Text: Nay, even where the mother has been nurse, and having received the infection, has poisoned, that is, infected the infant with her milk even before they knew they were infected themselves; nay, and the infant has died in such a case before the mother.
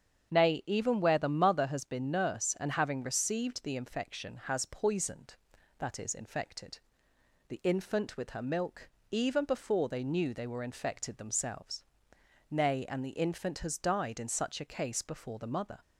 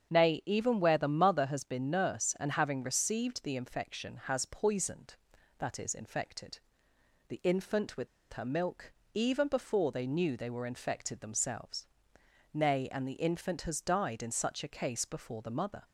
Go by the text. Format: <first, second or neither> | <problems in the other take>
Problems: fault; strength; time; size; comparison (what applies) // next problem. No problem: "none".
first | starts louder than the rest; strong; until 1.1 s; 7.5 dB; strong in the first // pauses between "infected" and "the"; noticeable; at 6.5 s; 0.70 s long; noticeable in the first // pauses between "with" and "her"; slight; at 8.0 s; 0.26 s long // pauses between "milk" and "even"; slight; at 8.9 s; 0.22 s long; slight in the first